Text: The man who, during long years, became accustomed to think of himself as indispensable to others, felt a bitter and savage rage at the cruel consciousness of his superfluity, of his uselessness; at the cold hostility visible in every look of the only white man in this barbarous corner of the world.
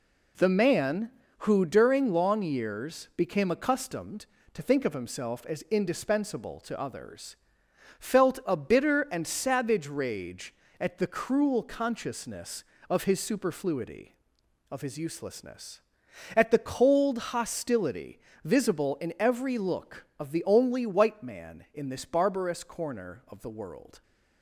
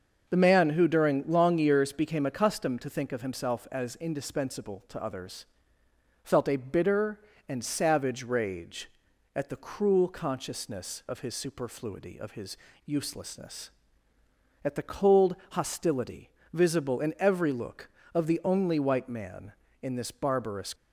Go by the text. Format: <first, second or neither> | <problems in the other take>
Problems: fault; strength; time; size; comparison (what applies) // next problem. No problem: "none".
first | starts louder than the rest; until 1.3 s; 6.5 dB // pauses between "his" and "uselessness"; slight; at 12.5 s; 0.30 s long // pauses between "cold" and "hostility"; slight; at 15.3 s; 0.16 s long // pauses between "hostility" and "visible"; slight; at 16.3 s; 0.20 s long; slight in the first // stops before "corner of the world"; at 20.7 s